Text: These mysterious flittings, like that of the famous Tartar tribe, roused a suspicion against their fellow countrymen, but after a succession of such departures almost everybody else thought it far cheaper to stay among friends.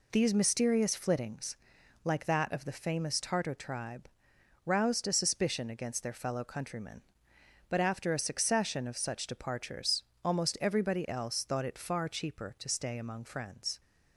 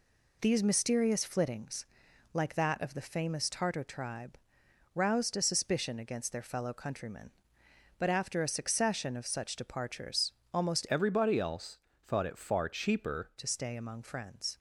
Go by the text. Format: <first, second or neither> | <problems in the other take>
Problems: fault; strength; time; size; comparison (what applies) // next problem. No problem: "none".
first | pauses between "departures" and "almost"; slight; at 10.3 s; 0.20 s long; slight in the first // changes voice from "everybody" to "cheaper"; from 10.8 to 13.3 s; 2.5 s long // pauses between "else" and "thought"; slight; at 11.7 s; 0.24 s long